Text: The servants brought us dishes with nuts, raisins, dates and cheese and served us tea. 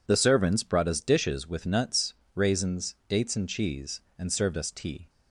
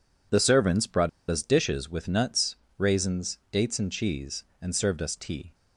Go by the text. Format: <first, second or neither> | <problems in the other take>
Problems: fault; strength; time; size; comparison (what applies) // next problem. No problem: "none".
first | pauses between "brought" and "us"; slight; at 1.0 s; 0.20 s long